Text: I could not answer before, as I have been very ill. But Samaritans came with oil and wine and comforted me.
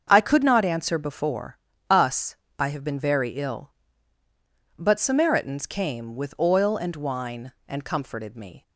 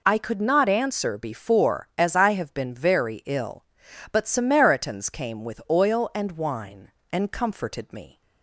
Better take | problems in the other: second | starts louder than the rest; until 1.1 s; 7 dB // says "us" for "as"; at 1.9 s

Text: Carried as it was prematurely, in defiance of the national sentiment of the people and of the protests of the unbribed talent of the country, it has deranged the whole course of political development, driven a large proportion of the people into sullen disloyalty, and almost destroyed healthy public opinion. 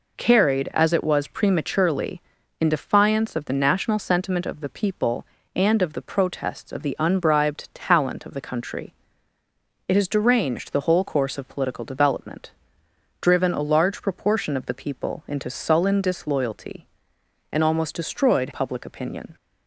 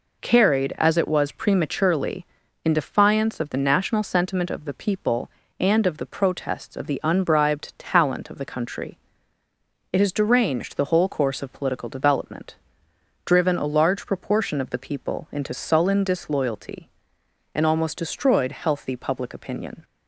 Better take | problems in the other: second | skips "healthy"; at 18.4 s

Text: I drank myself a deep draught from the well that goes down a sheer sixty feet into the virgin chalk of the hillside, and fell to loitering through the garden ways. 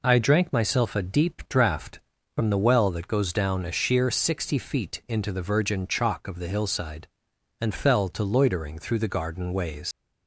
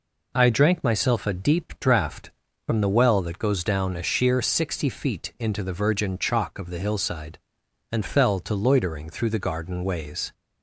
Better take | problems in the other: second | leaves "ways" unfinished; at 9.9 s; 105 ms

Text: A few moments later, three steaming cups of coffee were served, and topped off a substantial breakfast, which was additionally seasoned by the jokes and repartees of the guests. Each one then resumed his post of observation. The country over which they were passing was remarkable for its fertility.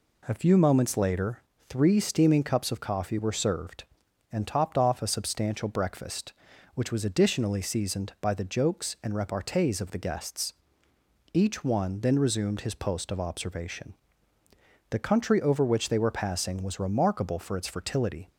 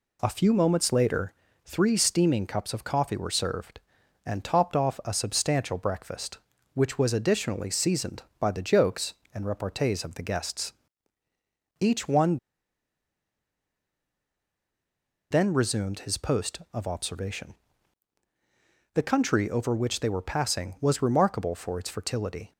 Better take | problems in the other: first | pauses between "one" and "then"; strong; at 12.3 s; 2.9 s long

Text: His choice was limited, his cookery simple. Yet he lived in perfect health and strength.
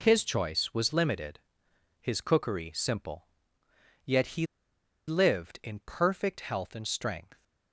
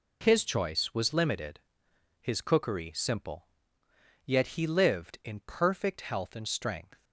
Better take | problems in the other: second | pauses between "he" and "lived"; noticeable; at 4.4 s; 0.62 s long

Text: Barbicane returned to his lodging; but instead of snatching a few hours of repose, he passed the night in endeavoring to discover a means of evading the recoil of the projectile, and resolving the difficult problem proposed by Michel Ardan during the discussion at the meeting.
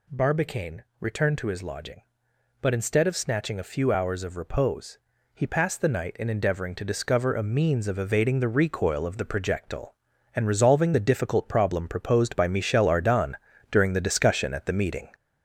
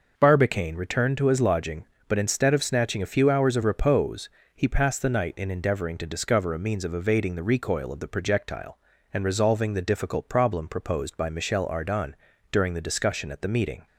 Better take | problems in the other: second | gets louder; noticeable; throughout; 5 dB // pauses between "Barbicane" and "returned"; slight; at 0.8 s; 0.16 s long // pauses between "Ardan" and "during"; at 13.3 s; 0.38 s long; also in the second

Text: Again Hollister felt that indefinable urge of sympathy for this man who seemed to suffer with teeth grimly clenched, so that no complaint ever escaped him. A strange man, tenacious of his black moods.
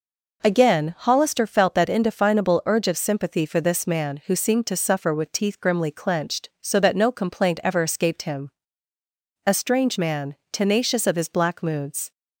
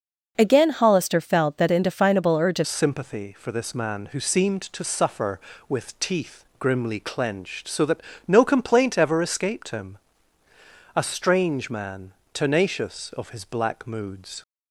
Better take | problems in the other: first | changes voice at "sympathy"; from 2.6 s on; 11.8 s long // pauses between "teeth" and "grimly"; slight; at 6.3 s; 0.18 s long // pauses between "that" and "no"; slight; at 7.9 s; 0.28 s long

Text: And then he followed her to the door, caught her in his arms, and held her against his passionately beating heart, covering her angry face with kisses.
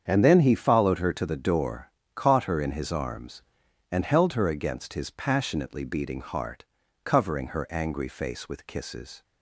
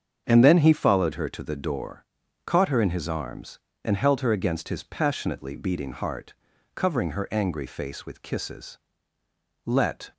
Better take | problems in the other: first | starts louder than the rest; strong; until 1.2 s; 7.5 dB; strong in the first // goes on to say "Let"; slight; from 9.6 s on; 0.48 s long

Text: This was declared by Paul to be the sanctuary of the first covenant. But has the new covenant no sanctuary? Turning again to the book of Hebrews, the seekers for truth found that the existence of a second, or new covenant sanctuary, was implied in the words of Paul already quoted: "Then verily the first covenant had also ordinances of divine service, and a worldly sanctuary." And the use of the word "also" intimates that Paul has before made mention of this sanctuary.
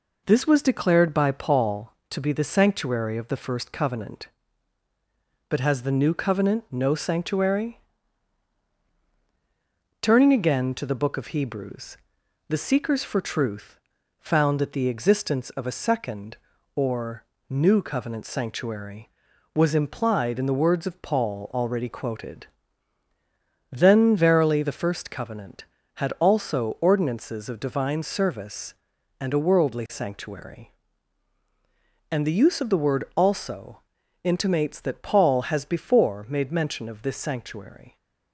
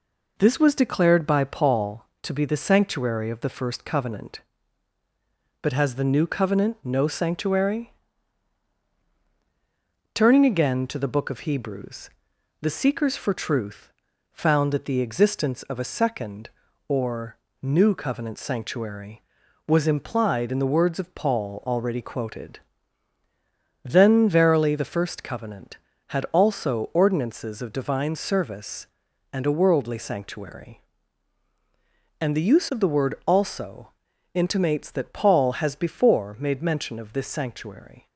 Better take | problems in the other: neither | pauses between "truth" and "found"; the same in both // pauses between "or" and "new"; slight; the same in both // pauses between "also" and "intimates"; the same in both

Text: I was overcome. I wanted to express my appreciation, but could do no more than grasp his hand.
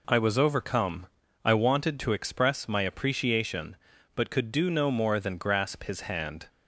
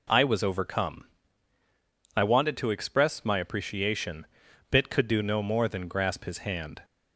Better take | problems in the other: first | says "bit" for "but"; at 4.7 s

